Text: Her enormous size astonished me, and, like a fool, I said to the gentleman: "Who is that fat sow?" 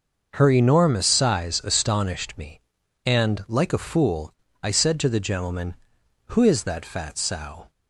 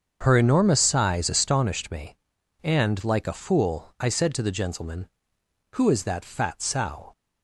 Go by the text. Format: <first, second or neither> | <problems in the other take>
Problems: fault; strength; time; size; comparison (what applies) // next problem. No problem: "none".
neither | starts louder than the rest; the same in both